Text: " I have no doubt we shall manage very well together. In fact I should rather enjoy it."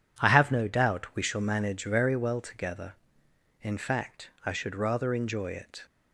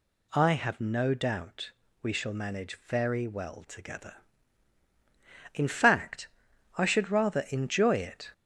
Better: first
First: pauses between "fact" and "I"; slight; at 4.3 s; 0.16 s long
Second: gets louder; slight; throughout; 3 dB // pauses between "doubt" and "we"; slight; at 1.7 s; 0.32 s long // pauses between "fact" and "I"; noticeable; at 6.2 s; 0.50 s long

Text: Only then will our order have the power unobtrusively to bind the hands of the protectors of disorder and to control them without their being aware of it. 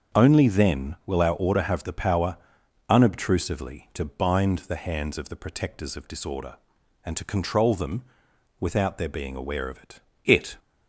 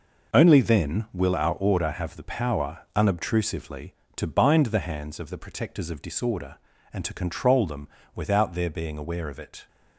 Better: second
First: starts louder than the rest; until 1.2 s; 7 dB // pauses between "power" and "unobtrusively"; noticeable; at 2.3 s; 0.54 s long // pauses between "them" and "without"; noticeable; at 8.0 s; 0.56 s long // says "it" twice; at 10.2 s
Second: pauses between "them" and "without"; slight; at 7.8 s; 0.26 s long

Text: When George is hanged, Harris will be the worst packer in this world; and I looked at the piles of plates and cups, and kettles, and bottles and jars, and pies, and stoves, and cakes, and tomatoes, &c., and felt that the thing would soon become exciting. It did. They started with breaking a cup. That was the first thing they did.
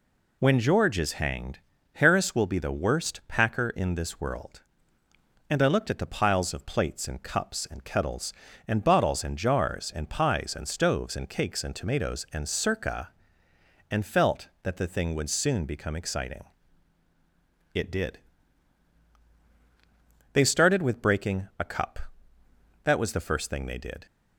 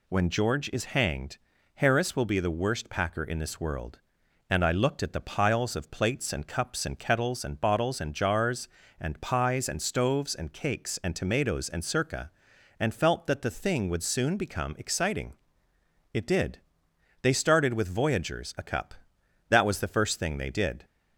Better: first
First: none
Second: says "voyagers" for "breaking"; at 17.8 s

